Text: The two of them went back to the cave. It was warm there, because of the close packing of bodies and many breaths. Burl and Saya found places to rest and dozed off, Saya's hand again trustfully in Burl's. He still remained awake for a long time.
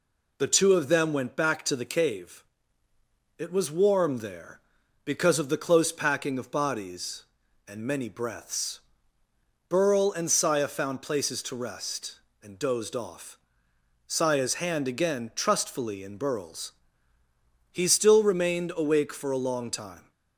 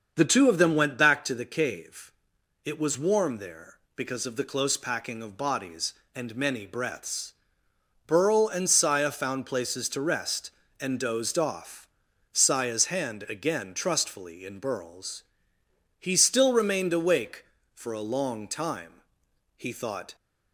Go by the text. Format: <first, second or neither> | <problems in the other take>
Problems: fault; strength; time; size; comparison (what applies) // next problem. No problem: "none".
first | starts louder than the rest; until 1.1 s; 7 dB // goes on to say "He thought"; from 19.5 s on; 0.58 s long